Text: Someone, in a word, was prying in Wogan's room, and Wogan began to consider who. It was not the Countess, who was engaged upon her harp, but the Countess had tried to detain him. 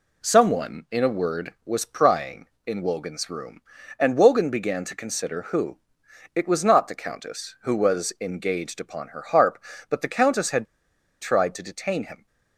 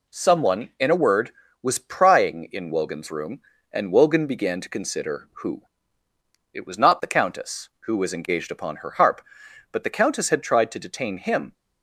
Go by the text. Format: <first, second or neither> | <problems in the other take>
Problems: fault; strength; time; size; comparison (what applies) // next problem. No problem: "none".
second | pauses between "had" and "tried"; noticeable; at 10.6 s; 0.56 s long